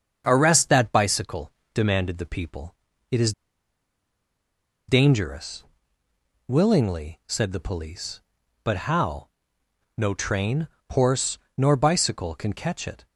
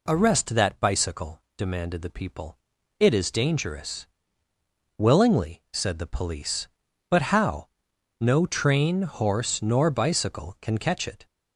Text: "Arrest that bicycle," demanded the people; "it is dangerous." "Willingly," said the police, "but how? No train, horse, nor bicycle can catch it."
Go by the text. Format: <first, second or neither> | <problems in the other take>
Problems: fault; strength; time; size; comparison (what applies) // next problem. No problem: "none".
second | starts louder than the rest; strong; until 1.2 s; 7 dB // pauses between "is" and "dangerous"; strong; at 3.3 s; 1.5 s long